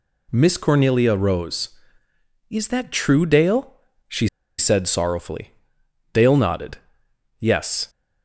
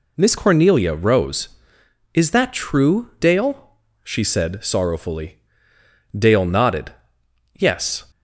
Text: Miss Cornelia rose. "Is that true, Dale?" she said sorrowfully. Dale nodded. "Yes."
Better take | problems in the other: second | pauses between "she" and "said"; slight; at 4.2 s; 0.30 s long

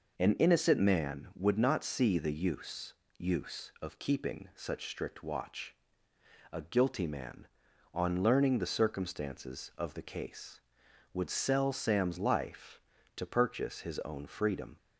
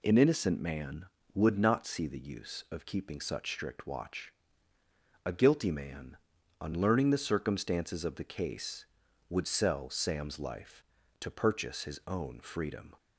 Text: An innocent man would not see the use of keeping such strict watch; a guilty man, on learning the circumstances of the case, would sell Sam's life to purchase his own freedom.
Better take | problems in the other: second | says "use" twice; at 3.1 s

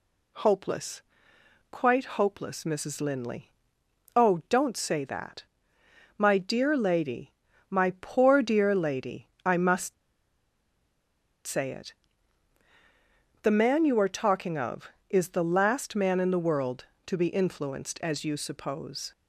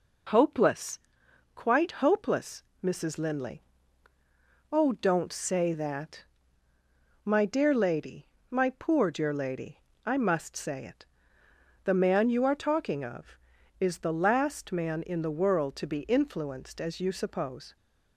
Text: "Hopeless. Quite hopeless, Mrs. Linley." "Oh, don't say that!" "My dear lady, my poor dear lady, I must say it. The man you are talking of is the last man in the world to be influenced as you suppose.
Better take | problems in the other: second | pauses between "must" and "say"; strong; at 9.9 s; 1.5 s long

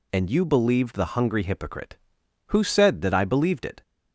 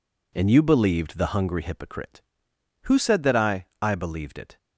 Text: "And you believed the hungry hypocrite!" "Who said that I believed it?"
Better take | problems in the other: first | says "I" twice; at 3.8 s

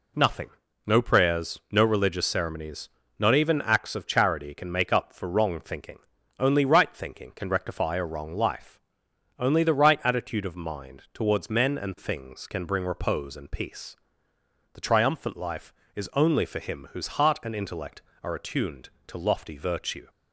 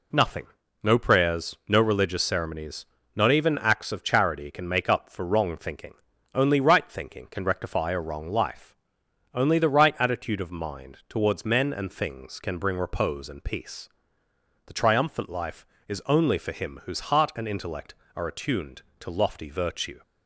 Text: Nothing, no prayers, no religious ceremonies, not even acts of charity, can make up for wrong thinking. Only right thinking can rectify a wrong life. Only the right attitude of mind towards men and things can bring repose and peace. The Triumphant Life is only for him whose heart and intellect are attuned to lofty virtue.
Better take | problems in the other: neither | none

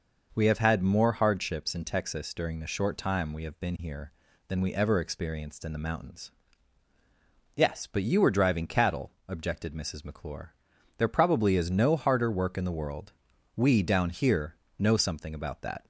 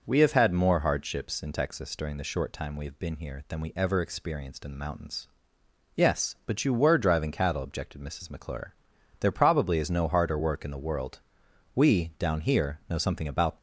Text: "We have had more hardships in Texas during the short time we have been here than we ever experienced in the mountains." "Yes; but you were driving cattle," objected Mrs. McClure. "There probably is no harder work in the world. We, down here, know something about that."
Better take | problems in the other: first | stops before "that"; at 13.5 s

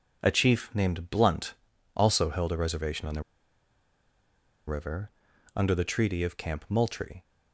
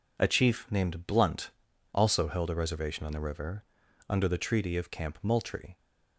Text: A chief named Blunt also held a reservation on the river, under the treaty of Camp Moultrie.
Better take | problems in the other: second | pauses between "Blunt" and "also"; at 1.5 s; 0.42 s long; also in the second // pauses between "the" and "river"; strong; at 3.2 s; 1.4 s long

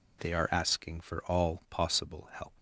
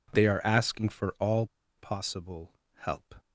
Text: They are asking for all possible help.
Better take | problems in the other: first | pauses between "all" and "possible"; slight; at 1.4 s; 0.32 s long // pauses between "possible" and "help"; slight; at 2.5 s; 0.24 s long

